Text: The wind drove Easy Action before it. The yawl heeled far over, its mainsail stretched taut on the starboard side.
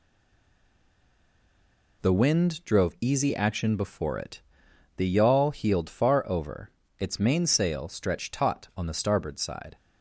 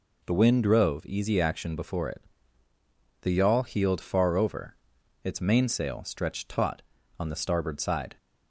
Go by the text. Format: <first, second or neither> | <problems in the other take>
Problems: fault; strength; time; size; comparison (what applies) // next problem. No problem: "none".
second | stays silent before the first word; noticeable; until 2.0 s; 2.0 s long